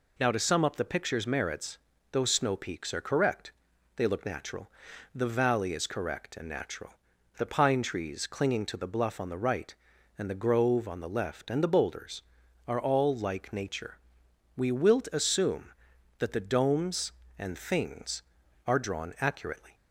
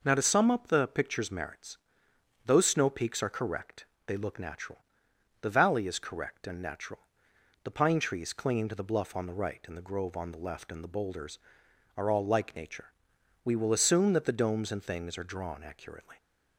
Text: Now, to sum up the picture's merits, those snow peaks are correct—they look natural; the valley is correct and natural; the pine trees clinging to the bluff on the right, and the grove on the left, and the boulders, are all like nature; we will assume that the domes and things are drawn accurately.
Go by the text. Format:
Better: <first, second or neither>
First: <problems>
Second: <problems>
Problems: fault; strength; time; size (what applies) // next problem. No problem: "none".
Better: second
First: says "wilt" for "will"; at 14.7 s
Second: none